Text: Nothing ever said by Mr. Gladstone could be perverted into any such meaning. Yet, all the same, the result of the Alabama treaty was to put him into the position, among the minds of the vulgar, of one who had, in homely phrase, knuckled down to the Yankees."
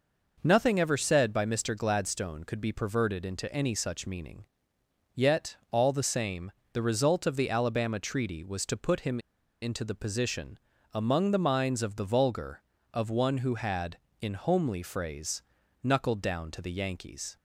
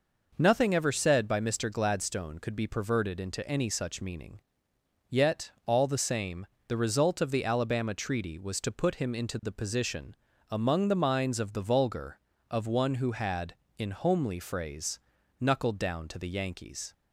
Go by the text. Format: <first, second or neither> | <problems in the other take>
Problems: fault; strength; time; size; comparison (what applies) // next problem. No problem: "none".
second | pauses between "him" and "into"; at 9.1 s; 0.43 s long